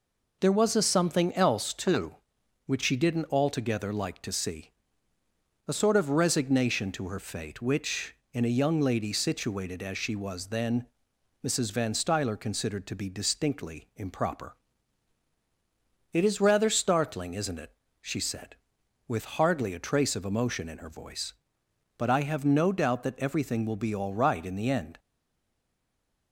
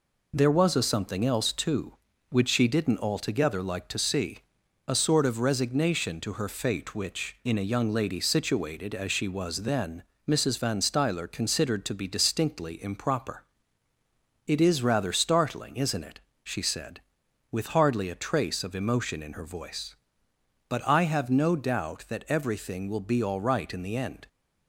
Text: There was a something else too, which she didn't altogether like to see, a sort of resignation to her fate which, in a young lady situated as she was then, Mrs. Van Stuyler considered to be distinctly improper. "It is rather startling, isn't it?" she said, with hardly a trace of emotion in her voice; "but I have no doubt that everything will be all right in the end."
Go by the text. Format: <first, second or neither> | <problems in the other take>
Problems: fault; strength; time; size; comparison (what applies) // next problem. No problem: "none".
second | stays silent after the last word; noticeable; from 24.9 s on; 1.4 s long